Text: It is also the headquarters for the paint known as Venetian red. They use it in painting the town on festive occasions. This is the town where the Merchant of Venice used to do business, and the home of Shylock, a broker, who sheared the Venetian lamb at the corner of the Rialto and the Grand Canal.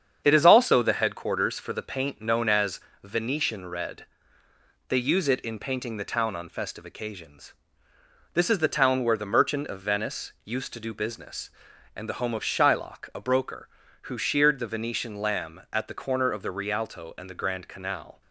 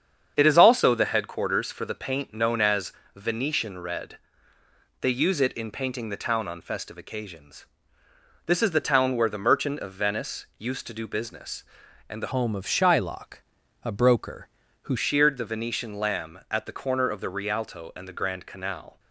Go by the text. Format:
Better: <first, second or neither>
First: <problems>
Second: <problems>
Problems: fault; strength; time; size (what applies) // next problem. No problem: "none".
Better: first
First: starts louder than the rest; strong; until 1.2 s; 8 dB // pauses between "as" and "Venetian"; slight; at 2.7 s; 0.24 s long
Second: starts louder than the rest; strong; until 1.3 s; 8 dB // pauses between "as" and "Venetian"; slight; at 2.9 s; 0.24 s long // changes voice from "home" to "who"; from 12.3 to 14.9 s; 2.6 s long